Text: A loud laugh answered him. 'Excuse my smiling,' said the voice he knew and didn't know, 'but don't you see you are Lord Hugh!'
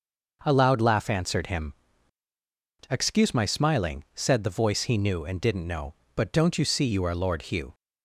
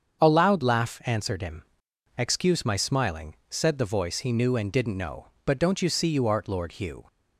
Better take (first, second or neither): first